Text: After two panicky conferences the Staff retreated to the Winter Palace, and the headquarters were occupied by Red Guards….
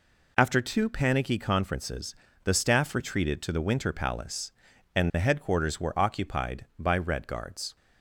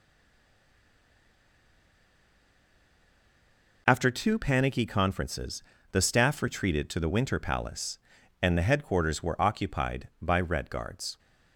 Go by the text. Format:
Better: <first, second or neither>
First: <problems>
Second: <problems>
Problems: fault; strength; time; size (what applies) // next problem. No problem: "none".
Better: first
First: pauses between "conferences" and "the"; slight; at 2.1 s; 0.28 s long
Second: stays silent before the first word; strong; until 3.8 s; 3.8 s long // pauses between "conferences" and "the"; slight; at 5.6 s; 0.28 s long